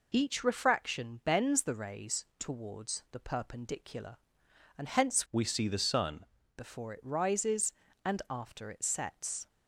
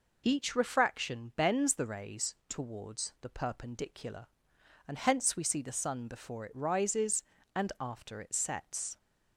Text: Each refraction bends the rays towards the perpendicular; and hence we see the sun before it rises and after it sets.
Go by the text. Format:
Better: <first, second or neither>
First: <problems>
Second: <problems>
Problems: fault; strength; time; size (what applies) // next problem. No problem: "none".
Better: second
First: changes voice from "we" to "sun"; from 5.3 to 6.2 s; 0.9 s long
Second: none